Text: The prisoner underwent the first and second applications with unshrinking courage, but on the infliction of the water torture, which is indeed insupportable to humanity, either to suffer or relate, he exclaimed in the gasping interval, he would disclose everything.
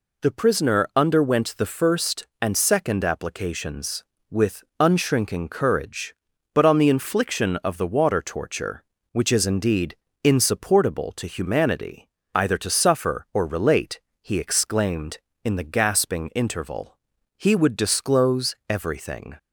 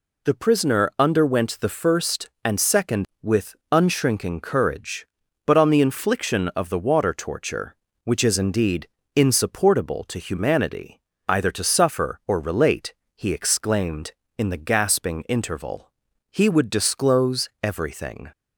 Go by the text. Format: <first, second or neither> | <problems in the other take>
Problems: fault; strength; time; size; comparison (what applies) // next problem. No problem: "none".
first | skips "applications"; at 3.1 s // pauses between "with" and "unshrinking"; slight; at 3.5 s; 0.16 s long; slight in the first // pauses between "indeed" and "insupportable"; slight; at 8.8 s; 0.28 s long; slight in the first